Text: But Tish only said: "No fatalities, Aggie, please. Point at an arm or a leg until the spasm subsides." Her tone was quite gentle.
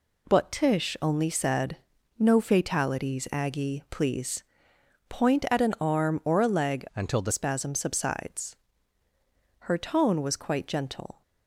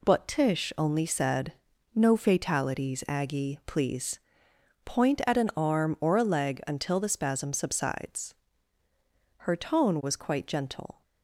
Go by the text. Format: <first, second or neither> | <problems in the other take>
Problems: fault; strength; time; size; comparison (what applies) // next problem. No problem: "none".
second | changes voice from "until" to "the"; from 6.9 to 7.3 s; 0.4 s long